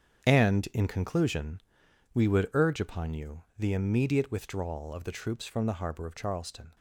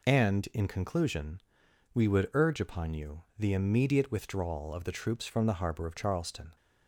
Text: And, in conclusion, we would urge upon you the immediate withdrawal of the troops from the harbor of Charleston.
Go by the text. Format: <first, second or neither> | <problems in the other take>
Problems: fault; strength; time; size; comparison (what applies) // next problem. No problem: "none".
second | gets quieter; strong; throughout; 10.5 dB